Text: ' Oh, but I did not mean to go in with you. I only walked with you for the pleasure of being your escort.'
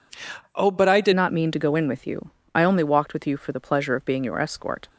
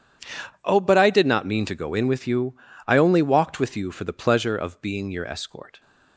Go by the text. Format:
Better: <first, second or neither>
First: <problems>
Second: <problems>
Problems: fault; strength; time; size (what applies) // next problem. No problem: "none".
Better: second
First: changes voice at "not"; from 1.1 s on; 3.7 s long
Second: none